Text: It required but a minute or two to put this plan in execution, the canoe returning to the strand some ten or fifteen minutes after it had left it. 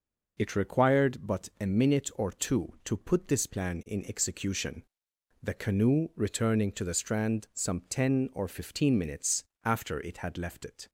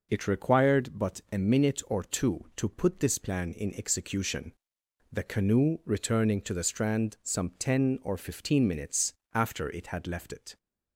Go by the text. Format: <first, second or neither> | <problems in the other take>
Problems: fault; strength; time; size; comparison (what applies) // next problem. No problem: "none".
neither | pauses between "minutes" and "after"; slight; the same in both